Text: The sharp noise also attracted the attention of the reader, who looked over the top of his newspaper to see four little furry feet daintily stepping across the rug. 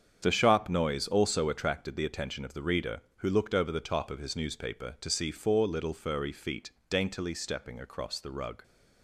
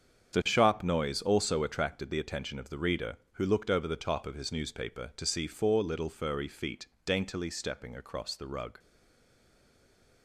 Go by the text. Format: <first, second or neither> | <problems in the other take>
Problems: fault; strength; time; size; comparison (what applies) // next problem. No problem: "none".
first | starts louder than the rest; strong; until 1.4 s; 8 dB; strong in the first // pauses between "feet" and "daintily"; slight; at 6.8 s; 0.20 s long; slight in the first // stays silent after the last word; noticeable; from 8.7 s on; 1.5 s long